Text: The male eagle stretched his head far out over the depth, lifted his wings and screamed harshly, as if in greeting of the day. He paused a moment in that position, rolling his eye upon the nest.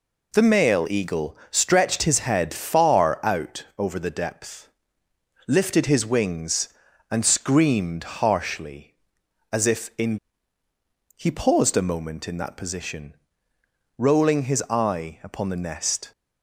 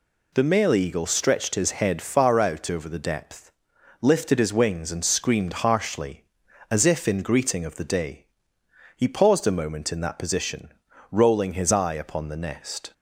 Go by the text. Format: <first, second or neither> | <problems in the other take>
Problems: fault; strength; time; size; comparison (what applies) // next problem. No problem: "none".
second | skips "greeting of the day"; at 10.6 s